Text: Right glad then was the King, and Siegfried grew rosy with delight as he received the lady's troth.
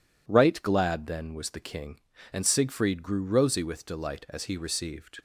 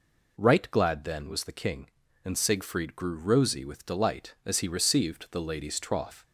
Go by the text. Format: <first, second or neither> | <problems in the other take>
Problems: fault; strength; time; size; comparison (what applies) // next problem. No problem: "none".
second | stops before "the lady's troth"; at 5.1 s